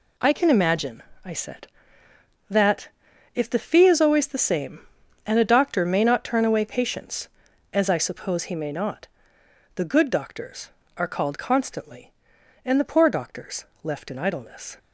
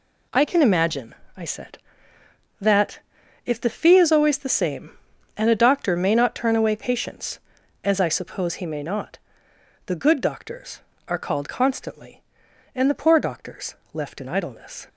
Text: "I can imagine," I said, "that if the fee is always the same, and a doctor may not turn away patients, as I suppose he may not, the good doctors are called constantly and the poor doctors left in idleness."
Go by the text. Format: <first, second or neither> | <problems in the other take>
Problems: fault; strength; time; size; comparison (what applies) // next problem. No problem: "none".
neither | pauses between "that" and "if"; noticeable; the same in both // pauses between "doctors" and "left"; slight; the same in both